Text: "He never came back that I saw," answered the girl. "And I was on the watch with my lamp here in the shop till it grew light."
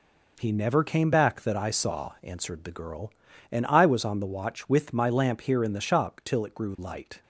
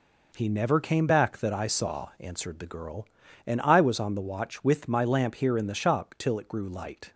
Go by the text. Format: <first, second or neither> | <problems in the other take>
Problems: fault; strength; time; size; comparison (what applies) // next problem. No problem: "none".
neither | none